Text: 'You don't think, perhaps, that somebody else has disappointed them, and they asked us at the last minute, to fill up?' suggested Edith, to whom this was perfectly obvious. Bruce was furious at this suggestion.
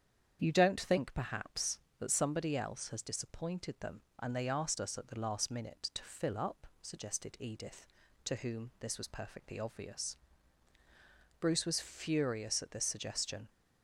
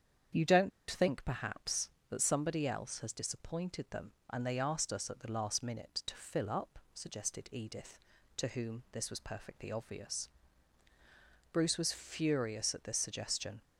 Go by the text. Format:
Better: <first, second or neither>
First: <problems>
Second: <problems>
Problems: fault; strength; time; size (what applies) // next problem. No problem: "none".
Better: first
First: starts louder than the rest; strong; until 1.4 s; 8.5 dB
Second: starts louder than the rest; strong; until 1.5 s; 8 dB // pauses between "don't" and "think"; slight; at 0.7 s; 0.20 s long